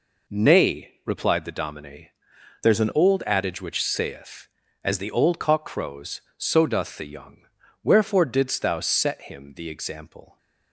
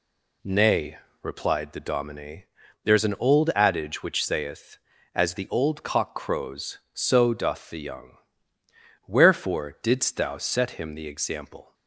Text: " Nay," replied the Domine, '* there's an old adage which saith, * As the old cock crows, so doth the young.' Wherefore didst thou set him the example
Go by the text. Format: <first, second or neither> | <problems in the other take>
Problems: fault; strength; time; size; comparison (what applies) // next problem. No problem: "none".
second | changes voice from "there's" to "an"; from 2.6 to 2.9 s; 0.3 s long